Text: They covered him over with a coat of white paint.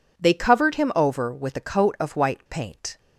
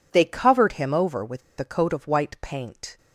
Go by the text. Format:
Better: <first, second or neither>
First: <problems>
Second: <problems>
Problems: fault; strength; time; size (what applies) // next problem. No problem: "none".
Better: first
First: none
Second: pauses between "with" and "a"; slight; at 1.4 s; 0.19 s long